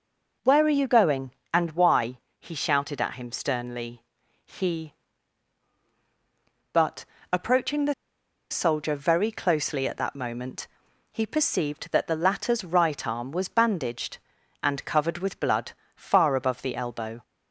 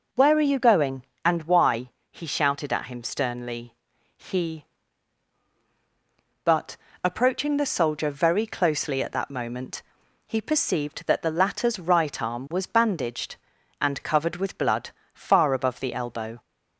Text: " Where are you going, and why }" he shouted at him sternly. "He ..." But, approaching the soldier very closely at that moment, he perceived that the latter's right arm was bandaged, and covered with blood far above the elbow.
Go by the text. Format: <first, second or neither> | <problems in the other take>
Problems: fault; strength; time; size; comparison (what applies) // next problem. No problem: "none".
second | starts louder than the rest; until 1.6 s; 6.5 dB; also in the second // pauses between "the" and "soldier"; noticeable; at 7.9 s; 0.57 s long // pauses between "blood" and "far"; slight; at 15.7 s; 0.24 s long; slight in the second